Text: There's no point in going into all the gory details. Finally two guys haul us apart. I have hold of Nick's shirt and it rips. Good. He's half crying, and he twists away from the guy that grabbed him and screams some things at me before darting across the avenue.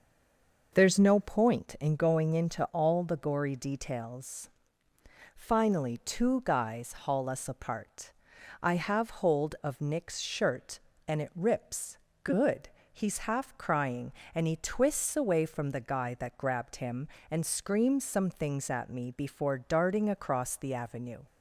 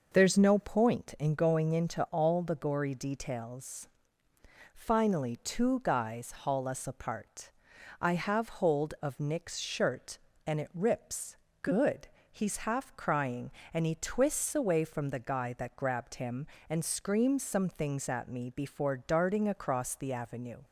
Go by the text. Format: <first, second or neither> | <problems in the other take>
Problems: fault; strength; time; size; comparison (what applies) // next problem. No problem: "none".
second | stays silent before the first word; slight; until 0.7 s; 0.7 s long